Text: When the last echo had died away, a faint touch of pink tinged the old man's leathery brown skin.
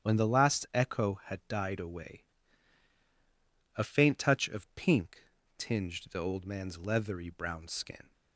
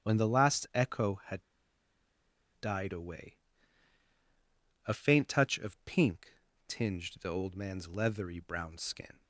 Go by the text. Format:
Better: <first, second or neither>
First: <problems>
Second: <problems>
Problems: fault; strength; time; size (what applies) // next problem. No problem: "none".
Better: first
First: starts louder than the rest; strong; until 1.1 s; 8.5 dB // pauses between "pink" and "tinged"; slight; at 5.2 s; 0.34 s long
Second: starts louder than the rest; strong; until 1.1 s; 8.5 dB // pauses between "had" and "died"; at 1.4 s; 1.1 s long // pauses between "pink" and "tinged"; slight; at 6.3 s; 0.34 s long